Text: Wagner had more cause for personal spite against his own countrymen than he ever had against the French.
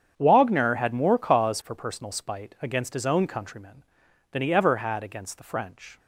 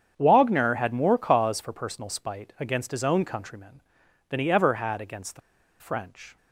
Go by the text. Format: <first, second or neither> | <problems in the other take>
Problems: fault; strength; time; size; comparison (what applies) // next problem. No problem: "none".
first | starts louder than the rest; strong; until 1.1 s; 8 dB; strong in the first // pauses between "the" and "French"; at 5.4 s; 0.40 s long